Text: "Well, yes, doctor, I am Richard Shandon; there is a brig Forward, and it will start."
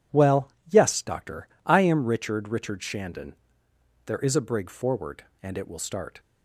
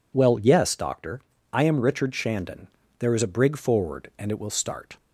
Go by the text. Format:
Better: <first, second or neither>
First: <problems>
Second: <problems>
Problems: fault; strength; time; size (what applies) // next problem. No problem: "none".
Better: second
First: says "Richard" twice; at 2.4 s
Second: none